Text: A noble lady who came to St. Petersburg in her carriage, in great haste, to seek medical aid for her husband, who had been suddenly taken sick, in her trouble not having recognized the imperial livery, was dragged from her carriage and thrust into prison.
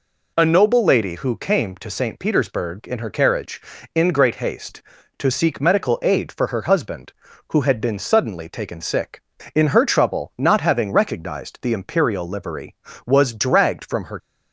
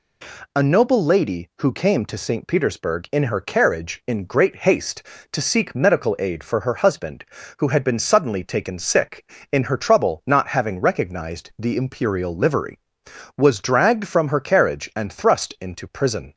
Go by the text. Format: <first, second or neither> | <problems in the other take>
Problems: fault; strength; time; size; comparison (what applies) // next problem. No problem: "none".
second | stops before "carriage and thrust into prison"; at 14.1 s